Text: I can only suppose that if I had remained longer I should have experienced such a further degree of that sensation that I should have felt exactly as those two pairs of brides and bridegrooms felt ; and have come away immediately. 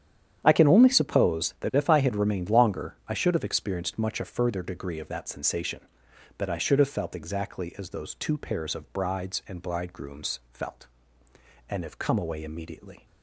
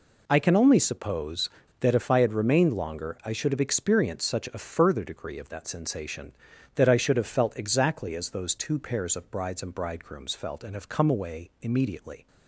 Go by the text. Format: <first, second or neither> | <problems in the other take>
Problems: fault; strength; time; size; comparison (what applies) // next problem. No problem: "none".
second | starts louder than the rest; strong; until 1.4 s; 9.5 dB // says "much" for "such"; at 3.9 s